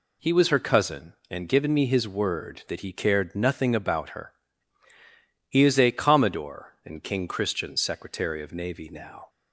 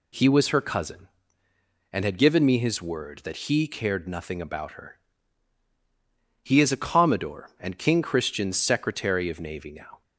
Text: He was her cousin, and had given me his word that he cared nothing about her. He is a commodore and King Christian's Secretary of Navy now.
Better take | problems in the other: second | skips "had"; at 1.4 s

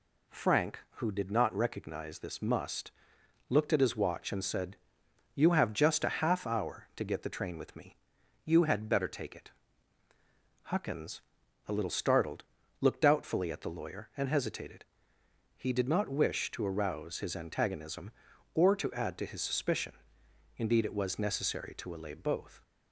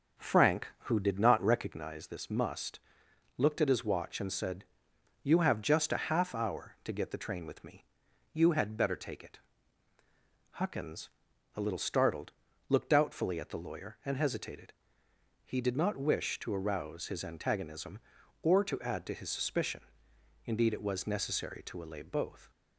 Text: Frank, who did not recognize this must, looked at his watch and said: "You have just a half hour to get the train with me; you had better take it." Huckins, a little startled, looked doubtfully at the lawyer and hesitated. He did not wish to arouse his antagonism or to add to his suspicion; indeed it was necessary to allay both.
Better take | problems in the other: first | starts louder than the rest; until 1.8 s; 7 dB

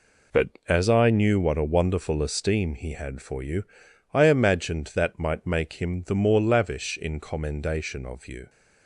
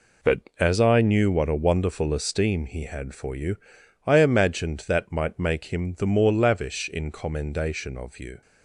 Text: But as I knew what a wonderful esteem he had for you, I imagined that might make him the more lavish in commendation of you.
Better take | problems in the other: neither | none

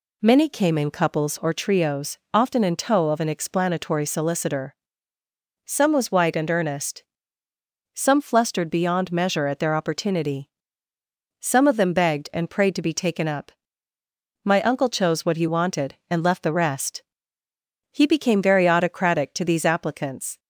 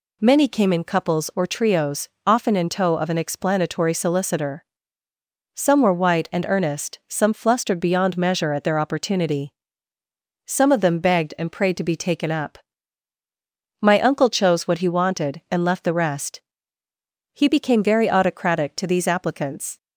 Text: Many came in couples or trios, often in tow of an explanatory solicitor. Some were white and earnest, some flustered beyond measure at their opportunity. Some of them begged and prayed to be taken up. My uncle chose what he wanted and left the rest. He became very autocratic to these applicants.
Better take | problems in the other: second | says "was" for "were"; at 5.9 s

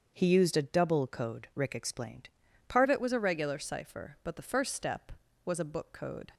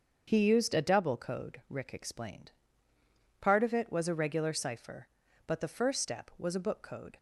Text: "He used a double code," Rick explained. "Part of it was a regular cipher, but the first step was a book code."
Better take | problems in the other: second | starts louder than the rest; until 1.1 s; 7 dB; also in the second // changes voice at "of"; from 2.8 s on; 3.5 s long

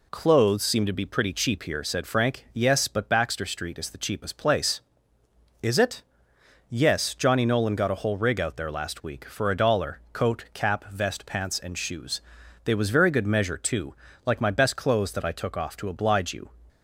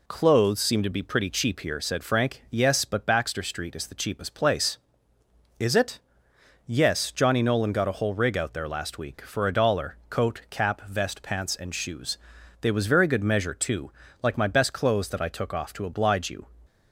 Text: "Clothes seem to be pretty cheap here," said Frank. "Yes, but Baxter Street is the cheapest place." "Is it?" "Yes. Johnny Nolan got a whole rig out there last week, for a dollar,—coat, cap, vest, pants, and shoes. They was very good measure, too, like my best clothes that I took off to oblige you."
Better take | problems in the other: neither | none

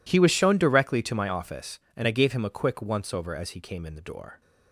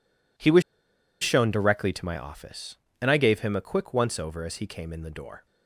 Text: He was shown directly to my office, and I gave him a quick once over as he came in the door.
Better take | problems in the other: first | pauses between "was" and "shown"; noticeable; at 0.6 s; 0.60 s long

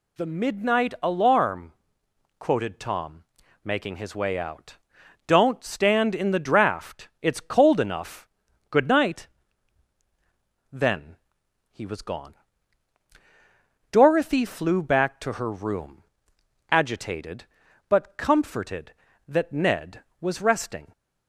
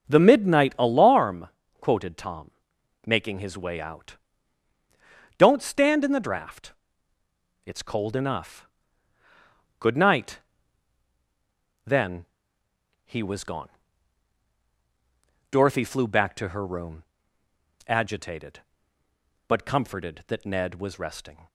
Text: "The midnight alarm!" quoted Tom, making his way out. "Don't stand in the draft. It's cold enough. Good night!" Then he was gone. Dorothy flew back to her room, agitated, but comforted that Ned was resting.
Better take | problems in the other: first | starts louder than the rest; until 1.1 s; 6 dB // pauses between "Then" and "he"; noticeable; at 12.2 s; 0.78 s long; noticeable in the first

